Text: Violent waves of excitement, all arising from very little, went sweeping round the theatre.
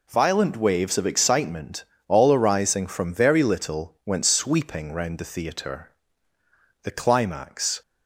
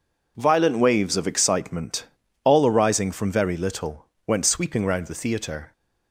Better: second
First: goes on to say "The climax"; noticeable; from 6.8 s on; 0.98 s long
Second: none

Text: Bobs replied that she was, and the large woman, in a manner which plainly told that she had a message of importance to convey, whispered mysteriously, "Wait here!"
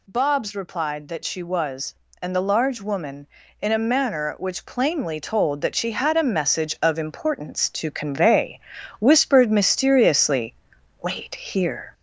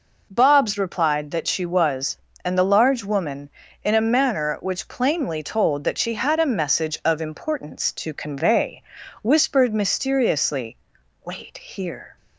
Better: second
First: gets louder; slight; throughout; 3 dB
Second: none

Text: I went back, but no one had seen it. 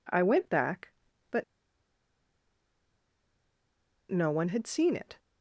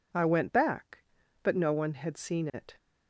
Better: second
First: pauses between "but" and "no"; strong; at 1.4 s; 2.6 s long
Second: none

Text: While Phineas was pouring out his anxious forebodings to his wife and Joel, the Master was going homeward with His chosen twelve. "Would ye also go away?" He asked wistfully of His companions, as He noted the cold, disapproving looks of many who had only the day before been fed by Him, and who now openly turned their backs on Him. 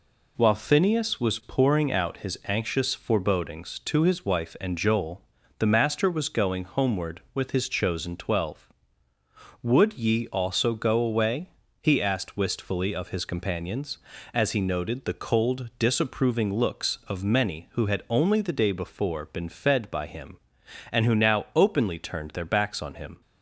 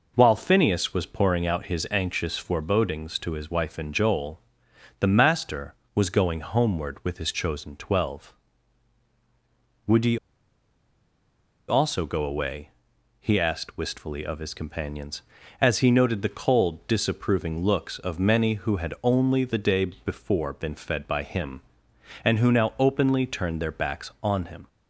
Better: first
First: none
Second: pauses between "ye" and "also"; strong; at 10.1 s; 1.5 s long

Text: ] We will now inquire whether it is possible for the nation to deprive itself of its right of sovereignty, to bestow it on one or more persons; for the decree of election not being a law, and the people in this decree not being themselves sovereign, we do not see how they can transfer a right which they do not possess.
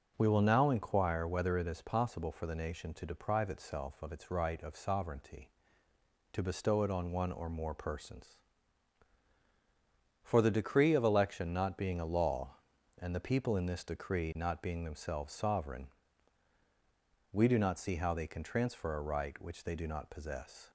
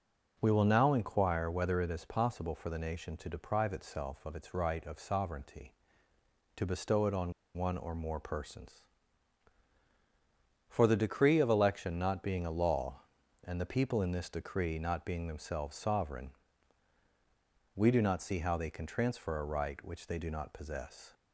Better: first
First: none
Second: pauses between "on" and "one"; slight; at 7.3 s; 0.22 s long

